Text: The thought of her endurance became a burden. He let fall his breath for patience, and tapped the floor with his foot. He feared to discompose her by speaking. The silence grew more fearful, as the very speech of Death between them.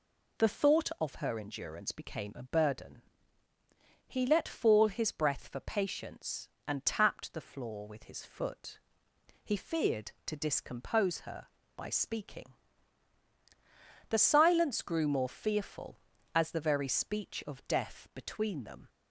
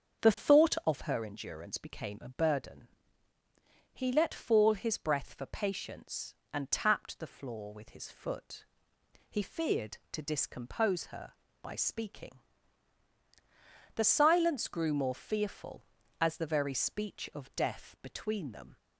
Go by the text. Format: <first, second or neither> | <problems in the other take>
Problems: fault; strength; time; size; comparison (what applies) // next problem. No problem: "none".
first | starts louder than the rest; strong; until 1.2 s; 7 dB